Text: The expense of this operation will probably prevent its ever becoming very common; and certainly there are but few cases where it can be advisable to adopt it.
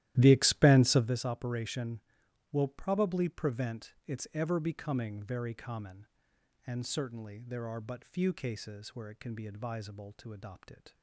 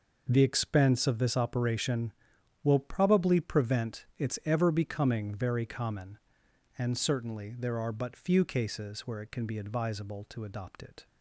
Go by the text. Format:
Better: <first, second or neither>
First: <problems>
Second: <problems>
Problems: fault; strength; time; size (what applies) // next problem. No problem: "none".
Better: second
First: starts louder than the rest; strong; until 1.2 s; 14 dB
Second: none